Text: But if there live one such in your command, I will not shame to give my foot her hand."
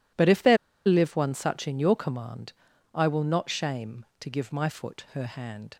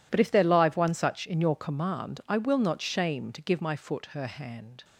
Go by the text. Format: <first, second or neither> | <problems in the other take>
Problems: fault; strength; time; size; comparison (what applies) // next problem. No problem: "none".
second | pauses between "there" and "live"; slight; at 0.5 s; 0.31 s long